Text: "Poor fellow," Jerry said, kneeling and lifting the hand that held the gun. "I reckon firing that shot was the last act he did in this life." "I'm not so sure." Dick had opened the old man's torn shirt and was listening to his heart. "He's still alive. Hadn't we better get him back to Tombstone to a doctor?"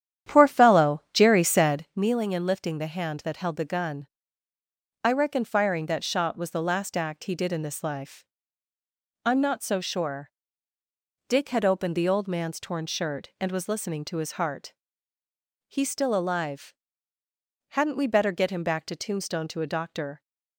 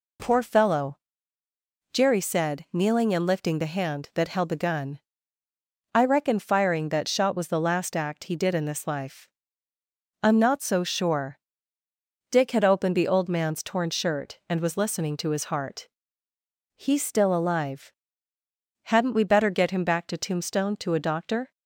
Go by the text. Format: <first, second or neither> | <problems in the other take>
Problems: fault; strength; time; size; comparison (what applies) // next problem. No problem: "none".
second | starts louder than the rest; strong; until 2.0 s; 10 dB